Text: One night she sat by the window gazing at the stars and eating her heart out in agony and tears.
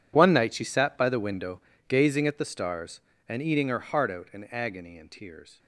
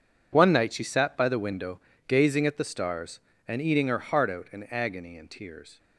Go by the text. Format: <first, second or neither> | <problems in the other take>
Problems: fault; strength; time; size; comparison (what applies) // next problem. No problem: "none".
second | gets quieter; strong; throughout; 17.5 dB // pauses between "window" and "gazing"; slight; at 1.6 s; 0.28 s long; slight in the second